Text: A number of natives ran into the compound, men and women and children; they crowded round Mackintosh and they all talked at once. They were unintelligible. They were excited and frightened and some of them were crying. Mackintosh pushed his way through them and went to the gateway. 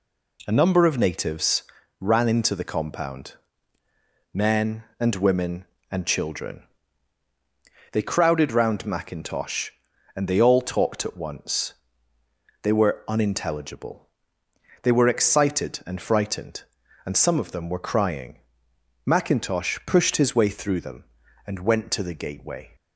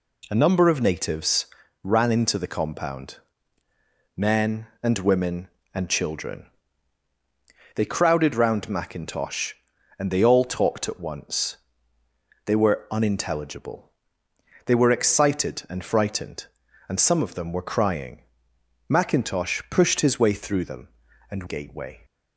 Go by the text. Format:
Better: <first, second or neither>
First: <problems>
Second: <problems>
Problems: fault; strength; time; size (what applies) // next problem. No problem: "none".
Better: first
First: pauses between "natives" and "ran"; at 1.6 s; 0.38 s long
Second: pauses between "natives" and "ran"; at 1.4 s; 0.38 s long // skips "went to the"; at 21.4 s